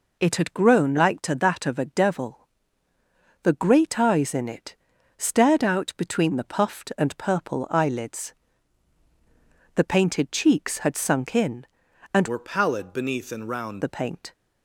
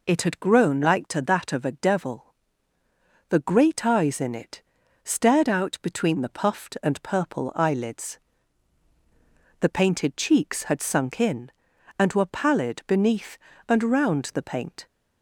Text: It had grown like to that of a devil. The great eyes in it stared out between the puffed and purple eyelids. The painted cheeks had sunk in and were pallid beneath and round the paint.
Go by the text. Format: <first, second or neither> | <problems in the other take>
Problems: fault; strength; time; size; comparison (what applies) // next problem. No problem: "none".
second | pauses between "it" and "stared"; at 4.7 s; 0.42 s long; also in the second // changes voice from "were" to "round"; from 12.2 to 13.8 s; 1.6 s long